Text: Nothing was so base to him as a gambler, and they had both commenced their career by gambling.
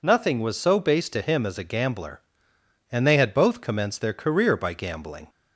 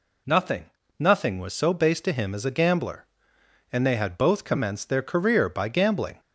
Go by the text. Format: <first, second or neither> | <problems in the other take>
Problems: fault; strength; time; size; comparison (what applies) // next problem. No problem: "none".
first | says "Nothing" twice; at 0.9 s